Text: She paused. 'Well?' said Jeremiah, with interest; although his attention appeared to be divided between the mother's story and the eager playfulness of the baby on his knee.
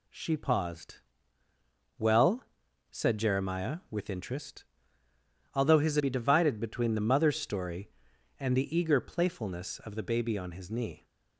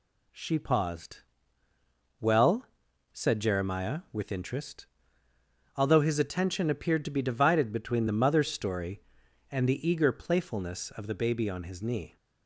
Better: second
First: skips "attention appeared to"; at 5.9 s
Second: none

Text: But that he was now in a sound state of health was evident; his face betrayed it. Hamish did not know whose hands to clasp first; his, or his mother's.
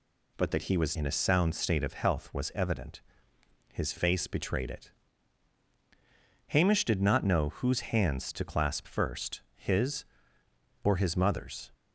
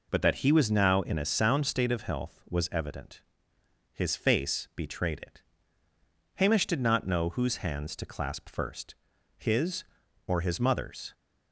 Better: second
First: skips "now"; at 0.9 s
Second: none

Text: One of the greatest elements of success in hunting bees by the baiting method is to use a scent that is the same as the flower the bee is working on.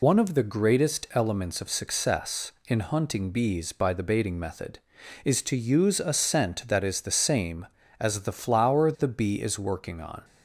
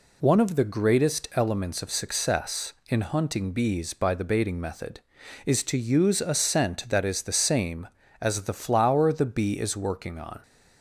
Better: second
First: loses the start of "One"; at 0.0 s; 35 ms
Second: none

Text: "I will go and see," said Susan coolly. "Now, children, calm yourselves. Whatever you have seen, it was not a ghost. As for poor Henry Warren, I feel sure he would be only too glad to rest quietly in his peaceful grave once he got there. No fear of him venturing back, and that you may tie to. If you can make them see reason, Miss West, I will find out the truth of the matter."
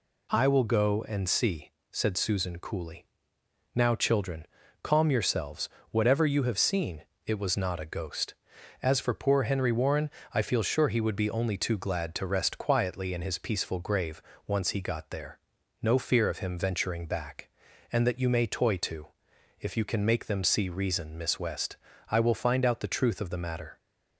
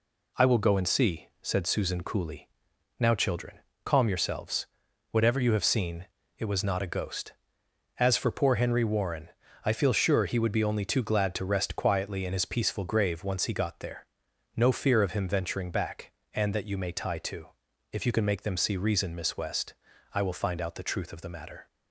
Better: second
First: pauses between "grave" and "once"; slight; at 14.1 s; 0.28 s long // says "toy" for "tie"; at 18.4 s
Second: none

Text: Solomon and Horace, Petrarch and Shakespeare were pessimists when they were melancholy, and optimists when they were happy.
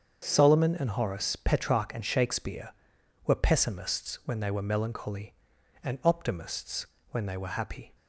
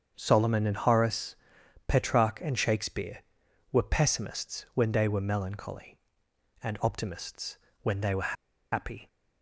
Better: first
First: starts louder than the rest; until 1.2 s; 7 dB // pauses between "optimists" and "when"; slight; at 6.8 s; 0.24 s long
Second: starts louder than the rest; until 1.1 s; 7 dB // pauses between "optimists" and "when"; slight; at 7.5 s; 0.26 s long // pauses between "were" and "happy"; at 8.3 s; 0.39 s long

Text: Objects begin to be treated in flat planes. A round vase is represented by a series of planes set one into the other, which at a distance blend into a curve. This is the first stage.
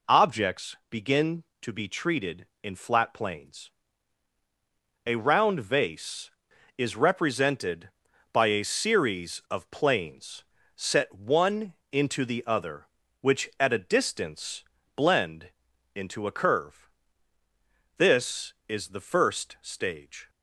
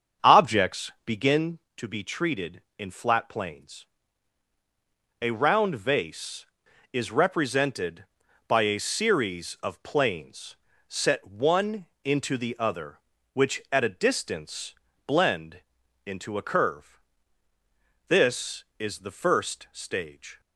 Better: first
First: pauses between "planes" and "set"; slight; at 10.4 s; 0.34 s long // pauses between "one" and "into"; slight; at 11.7 s; 0.18 s long // pauses between "distance" and "blend"; slight; at 14.6 s; 0.32 s long // pauses between "blend" and "into"; noticeable; at 15.4 s; 0.46 s long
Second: starts louder than the rest; strong; until 1.4 s; 7.5 dB // pauses between "planes" and "set"; slight; at 10.5 s; 0.34 s long // pauses between "one" and "into"; slight; at 11.8 s; 0.18 s long // pauses between "distance" and "blend"; slight; at 14.7 s; 0.32 s long // pauses between "blend" and "into"; noticeable; at 15.5 s; 0.46 s long

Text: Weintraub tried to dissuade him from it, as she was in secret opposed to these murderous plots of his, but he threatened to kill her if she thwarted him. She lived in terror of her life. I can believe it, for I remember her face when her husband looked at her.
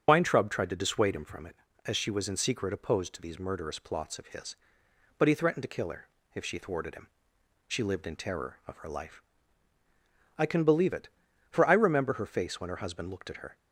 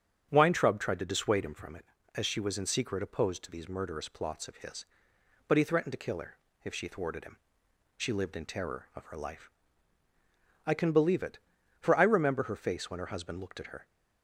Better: second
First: loses the start of "Weintraub"; at 0.0 s; 75 ms // starts louder than the rest; strong; until 1.0 s; 7.5 dB // pauses between "her" and "if"; slight; at 6.0 s; 0.28 s long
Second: starts louder than the rest; strong; until 1.3 s; 8 dB // pauses between "her" and "if"; slight; at 6.3 s; 0.28 s long

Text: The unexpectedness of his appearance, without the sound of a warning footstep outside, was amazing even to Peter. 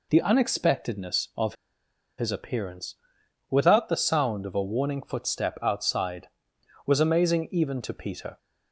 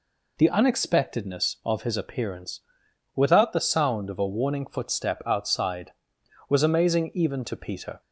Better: second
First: pauses between "of" and "his"; noticeable; at 1.5 s; 0.63 s long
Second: none

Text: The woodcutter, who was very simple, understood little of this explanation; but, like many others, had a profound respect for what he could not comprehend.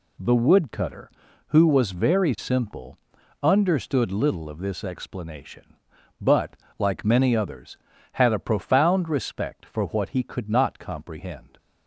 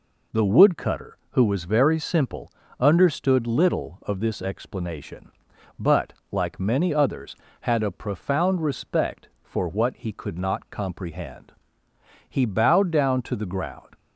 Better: first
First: none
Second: goes on to say "He bowed down to the ground"; from 12.2 s on; 1.6 s long

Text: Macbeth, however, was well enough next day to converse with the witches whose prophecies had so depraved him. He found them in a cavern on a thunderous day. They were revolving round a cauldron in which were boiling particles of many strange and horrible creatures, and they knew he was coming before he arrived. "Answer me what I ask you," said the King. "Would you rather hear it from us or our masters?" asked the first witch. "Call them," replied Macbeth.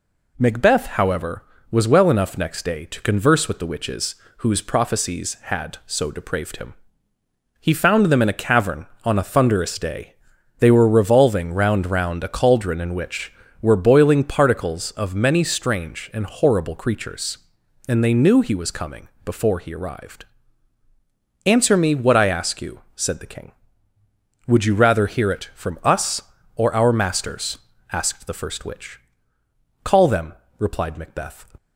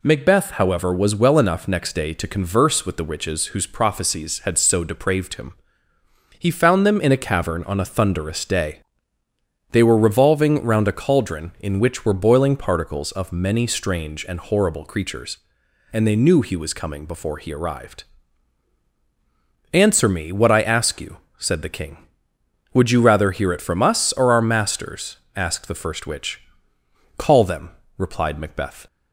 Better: second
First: pauses between "witches" and "whose"; slight; at 4.1 s; 0.22 s long // says "round" twice; at 11.8 s // pauses between "coming" and "before"; slight; at 19.0 s; 0.16 s long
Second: none

